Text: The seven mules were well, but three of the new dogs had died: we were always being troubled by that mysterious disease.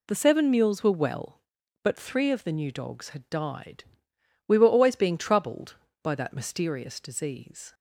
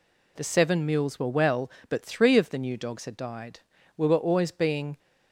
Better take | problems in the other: first | stops before "troubled by that mysterious disease"; at 4.9 s

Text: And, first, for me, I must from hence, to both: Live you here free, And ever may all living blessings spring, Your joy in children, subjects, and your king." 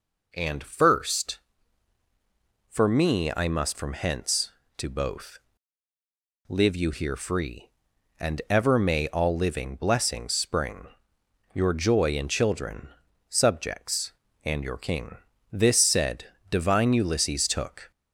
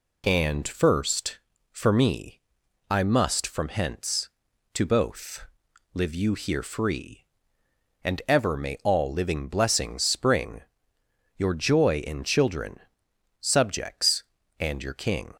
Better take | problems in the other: second | goes on to say "This said divine Ulysses took"; strong; from 15.5 s on; 2.3 s long

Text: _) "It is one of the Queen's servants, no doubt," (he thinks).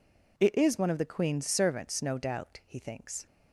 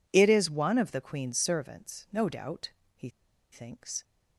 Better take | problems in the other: first | pauses between "he" and "thinks"; at 3.1 s; 0.41 s long

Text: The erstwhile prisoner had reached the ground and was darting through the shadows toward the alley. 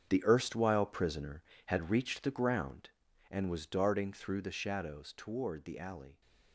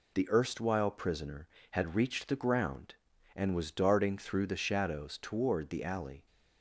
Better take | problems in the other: second | gets quieter; strong; throughout; 12 dB

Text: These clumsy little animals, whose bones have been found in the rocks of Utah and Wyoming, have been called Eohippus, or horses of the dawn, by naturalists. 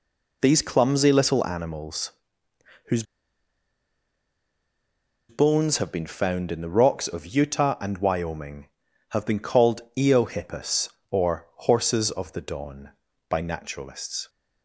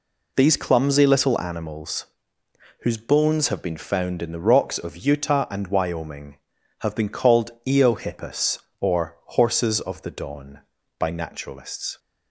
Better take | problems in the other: second | pauses between "whose" and "bones"; strong; at 3.0 s; 2.2 s long // pauses between "called" and "Eohippus"; slight; at 9.8 s; 0.16 s long; slight in the second

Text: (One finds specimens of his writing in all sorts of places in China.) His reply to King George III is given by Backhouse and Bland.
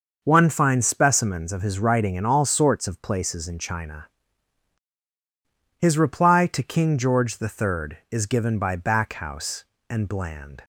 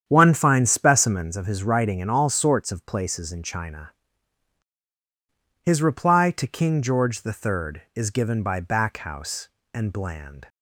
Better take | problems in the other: first | starts louder than the rest; strong; until 1.4 s; 8.5 dB

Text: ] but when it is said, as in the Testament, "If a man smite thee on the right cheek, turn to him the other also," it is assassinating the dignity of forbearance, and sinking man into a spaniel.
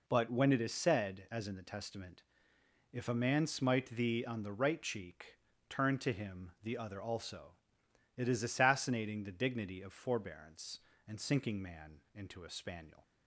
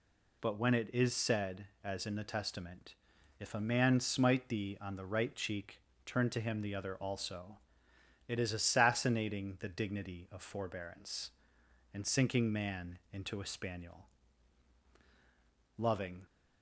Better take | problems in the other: first | goes on to say "Loving"; slight; from 15.7 s on; 0.48 s long

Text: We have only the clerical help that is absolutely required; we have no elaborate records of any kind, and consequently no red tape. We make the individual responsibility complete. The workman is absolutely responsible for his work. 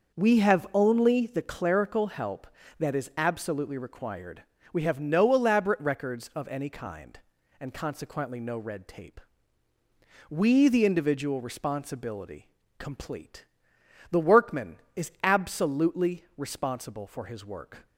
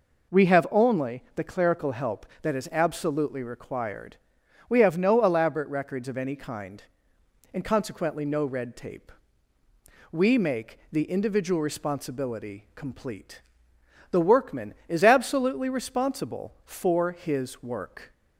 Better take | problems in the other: second | starts louder than the rest; noticeable; until 1.2 s; 6 dB // skips "make"; at 10.6 s // pauses between "responsibility" and "complete"; slight; at 12.4 s; 0.28 s long

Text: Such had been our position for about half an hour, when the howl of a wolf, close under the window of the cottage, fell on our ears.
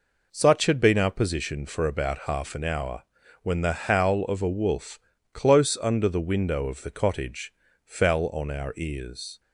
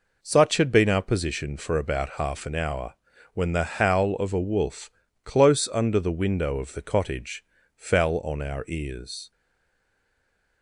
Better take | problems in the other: first | stays silent after the last word; noticeable; from 9.3 s on; 1.3 s long

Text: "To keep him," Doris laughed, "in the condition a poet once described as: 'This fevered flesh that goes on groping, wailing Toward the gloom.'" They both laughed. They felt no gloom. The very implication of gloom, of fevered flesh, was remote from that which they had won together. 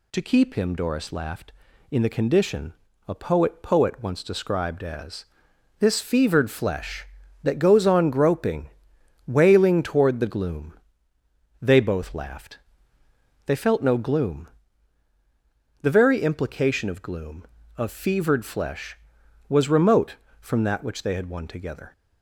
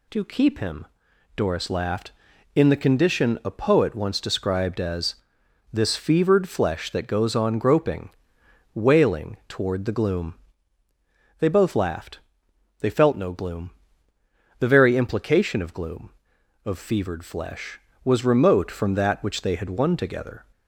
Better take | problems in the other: second | pauses between "condition" and "a"; slight; at 2.7 s; 0.34 s long // says "poet" twice; at 3.6 s

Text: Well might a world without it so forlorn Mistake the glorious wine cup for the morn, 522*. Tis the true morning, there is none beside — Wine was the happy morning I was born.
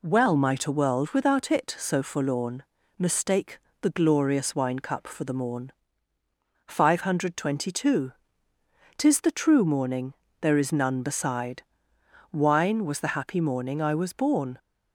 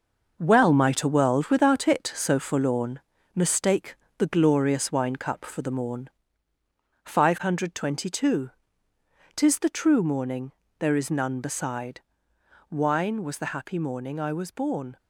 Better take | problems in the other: first | gets quieter; strong; throughout; 8 dB // pauses between "forlorn" and "Mistake"; slight; at 2.9 s; 0.36 s long; slight in the first // pauses between "Mistake" and "the"; slight; at 3.9 s; 0.22 s long; slight in the first

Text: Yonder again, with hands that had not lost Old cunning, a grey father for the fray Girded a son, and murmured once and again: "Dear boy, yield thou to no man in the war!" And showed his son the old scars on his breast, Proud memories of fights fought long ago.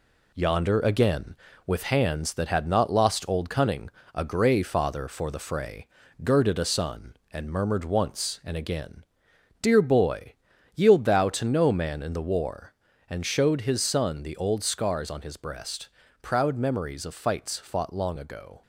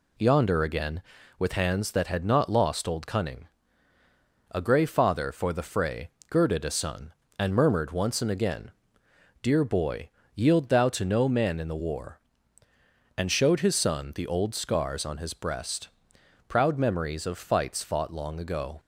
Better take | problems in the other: second | gets quieter; noticeable; throughout; 5.5 dB // pauses between "fray" and "Girded"; slight; at 5.8 s; 0.36 s long; slight in the second

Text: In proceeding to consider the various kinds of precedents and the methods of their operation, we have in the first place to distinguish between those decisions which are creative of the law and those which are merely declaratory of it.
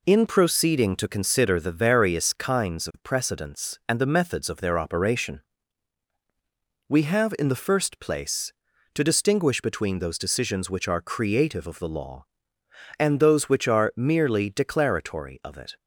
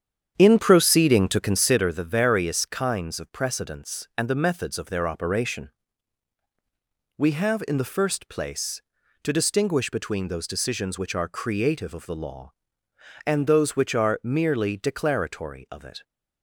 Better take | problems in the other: first | starts louder than the rest; strong; until 1.9 s; 8.5 dB

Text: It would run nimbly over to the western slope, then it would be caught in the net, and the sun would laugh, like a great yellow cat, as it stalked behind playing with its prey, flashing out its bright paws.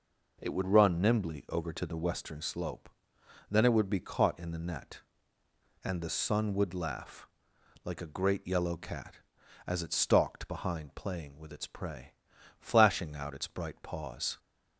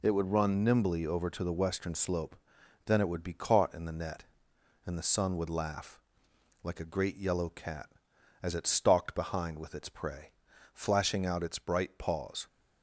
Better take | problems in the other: first | skips "playing"; at 9.5 s

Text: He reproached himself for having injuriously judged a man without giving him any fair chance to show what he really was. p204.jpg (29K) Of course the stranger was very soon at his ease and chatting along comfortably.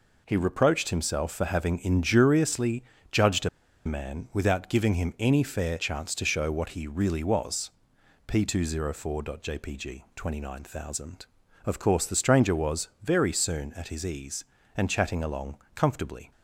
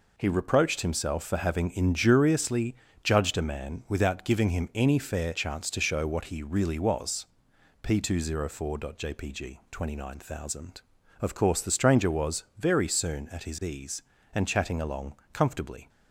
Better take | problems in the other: second | pauses between "injuriously" and "judged"; slight; at 2.8 s; 0.30 s long; slight in the second // pauses between "a" and "man"; at 3.4 s; 0.37 s long // pauses between "along" and "comfortably"; slight; at 15.5 s; 0.18 s long; slight in the second

